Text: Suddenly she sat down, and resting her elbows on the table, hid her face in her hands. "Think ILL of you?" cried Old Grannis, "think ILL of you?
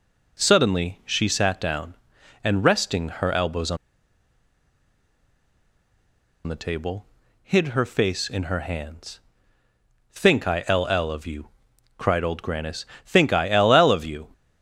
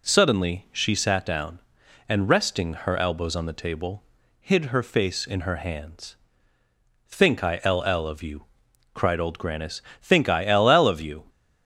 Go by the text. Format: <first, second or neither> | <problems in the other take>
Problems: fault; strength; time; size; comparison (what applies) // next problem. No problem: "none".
second | pauses between "on" and "the"; strong; at 3.7 s; 2.7 s long